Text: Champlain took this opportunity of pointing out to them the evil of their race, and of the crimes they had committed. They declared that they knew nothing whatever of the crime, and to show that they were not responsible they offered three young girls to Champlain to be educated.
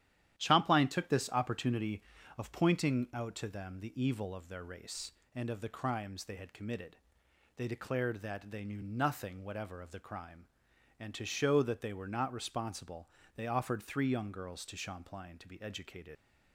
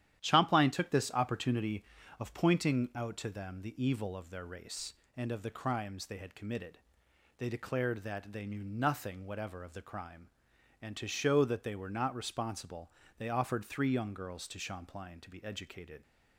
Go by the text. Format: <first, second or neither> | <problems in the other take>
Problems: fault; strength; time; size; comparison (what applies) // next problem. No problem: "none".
second | starts louder than the rest; strong; until 1.4 s; 11.5 dB; strong in the second // pauses between "responsible" and "they"; slight; at 13.0 s; 0.28 s long; slight in the second // leaves "educated" unfinished; at 16.1 s; 45 ms